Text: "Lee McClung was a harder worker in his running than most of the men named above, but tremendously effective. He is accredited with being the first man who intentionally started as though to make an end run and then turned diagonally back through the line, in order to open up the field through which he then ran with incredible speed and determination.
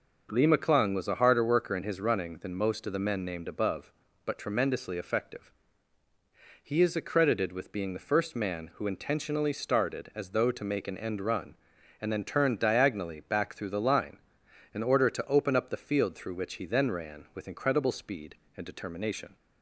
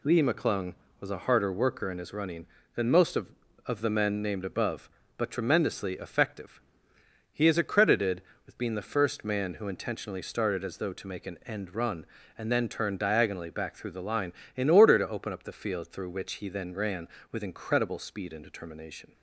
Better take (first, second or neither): first